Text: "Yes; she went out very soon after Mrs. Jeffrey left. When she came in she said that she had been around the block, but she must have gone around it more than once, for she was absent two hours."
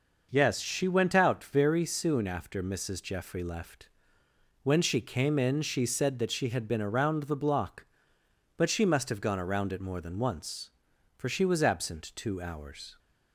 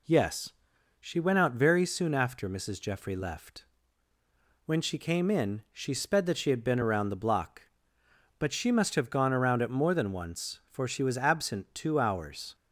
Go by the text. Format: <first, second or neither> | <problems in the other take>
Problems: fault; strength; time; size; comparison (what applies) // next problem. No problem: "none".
first | says "sped" for "said"; at 5.9 s